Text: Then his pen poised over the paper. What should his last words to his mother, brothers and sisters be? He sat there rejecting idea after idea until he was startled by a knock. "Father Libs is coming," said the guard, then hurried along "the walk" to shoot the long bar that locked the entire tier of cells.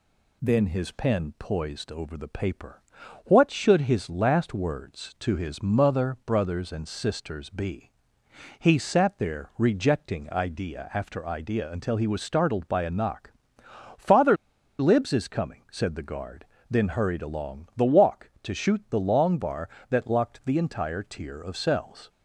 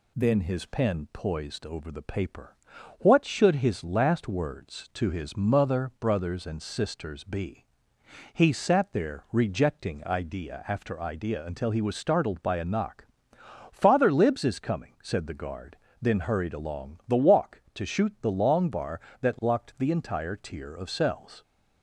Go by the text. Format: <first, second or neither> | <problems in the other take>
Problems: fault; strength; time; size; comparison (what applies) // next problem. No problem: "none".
second | pauses between "Father" and "Libs"; at 14.3 s; 0.44 s long